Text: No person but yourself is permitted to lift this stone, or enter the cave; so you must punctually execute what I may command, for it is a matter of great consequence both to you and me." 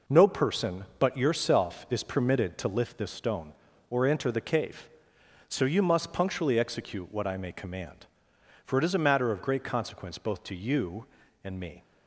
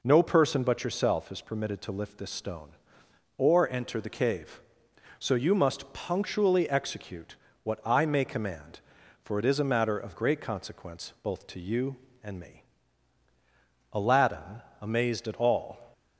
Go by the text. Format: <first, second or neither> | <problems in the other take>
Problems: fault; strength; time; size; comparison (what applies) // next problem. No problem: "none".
first | pauses between "execute" and "what"; slight; at 7.3 s; 0.28 s long // goes on to say "Aladdin amazed at all"; strong; from 13.9 s on; 1.9 s long